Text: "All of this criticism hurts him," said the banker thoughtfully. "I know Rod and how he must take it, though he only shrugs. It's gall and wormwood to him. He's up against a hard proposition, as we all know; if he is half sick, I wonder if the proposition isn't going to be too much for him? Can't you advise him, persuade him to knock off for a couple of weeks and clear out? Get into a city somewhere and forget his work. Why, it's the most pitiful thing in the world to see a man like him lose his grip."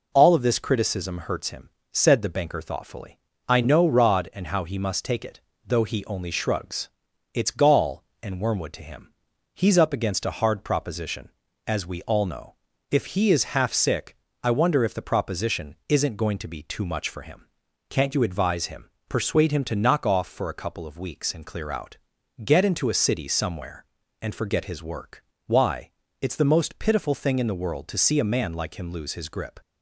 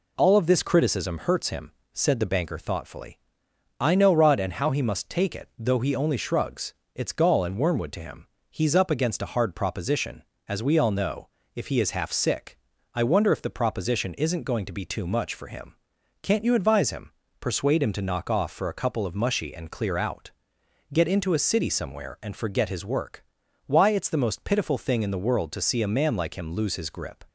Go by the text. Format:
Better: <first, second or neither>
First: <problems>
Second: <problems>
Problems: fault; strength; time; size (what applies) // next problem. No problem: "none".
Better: first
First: none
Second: says "mushy" for "weeks"; at 19.1 s